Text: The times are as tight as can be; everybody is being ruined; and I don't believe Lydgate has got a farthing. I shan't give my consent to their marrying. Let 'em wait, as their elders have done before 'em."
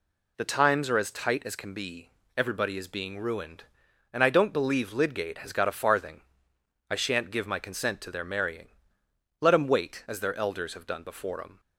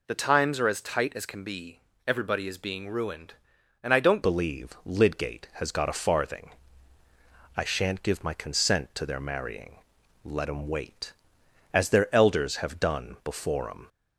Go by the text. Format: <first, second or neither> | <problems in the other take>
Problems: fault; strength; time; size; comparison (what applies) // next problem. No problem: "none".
first | changes voice at "believe"; from 4.2 s on; 9.6 s long